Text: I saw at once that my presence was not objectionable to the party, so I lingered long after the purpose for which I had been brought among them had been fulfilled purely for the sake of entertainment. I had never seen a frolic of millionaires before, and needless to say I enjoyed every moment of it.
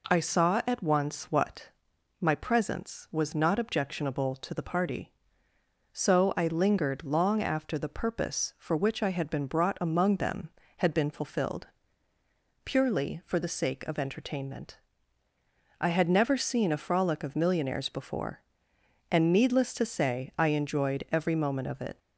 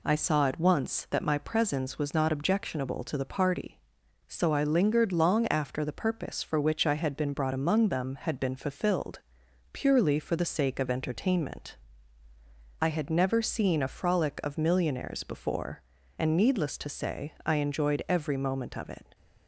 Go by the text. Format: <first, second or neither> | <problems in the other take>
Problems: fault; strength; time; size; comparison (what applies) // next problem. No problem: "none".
second | says "what" for "that"; at 1.3 s // pauses between "fulfilled" and "purely"; noticeable; at 11.6 s; 0.98 s long; noticeable in the second